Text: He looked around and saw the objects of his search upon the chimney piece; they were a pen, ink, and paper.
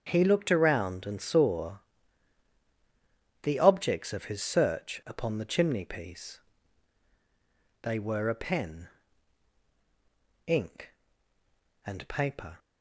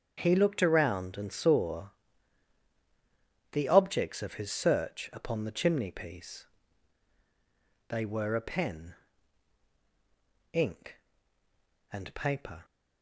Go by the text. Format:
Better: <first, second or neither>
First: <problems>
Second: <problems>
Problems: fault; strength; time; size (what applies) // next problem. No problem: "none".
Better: neither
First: starts louder than the rest; strong; until 1.0 s; 7.5 dB // pauses between "saw" and "the"; strong; at 1.7 s; 1.6 s long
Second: starts louder than the rest; strong; until 1.1 s; 7.5 dB // pauses between "saw" and "the"; strong; at 1.9 s; 1.6 s long